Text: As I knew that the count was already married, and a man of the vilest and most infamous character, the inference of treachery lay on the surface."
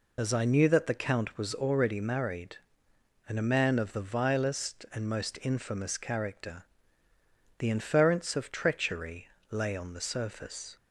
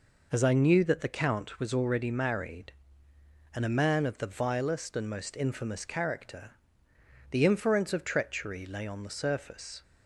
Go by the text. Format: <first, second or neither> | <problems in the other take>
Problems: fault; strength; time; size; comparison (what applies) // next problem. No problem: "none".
second | loses the start of "As"; at 0.1 s; 65 ms // pauses between "treachery" and "lay"; slight; at 9.2 s; 0.22 s long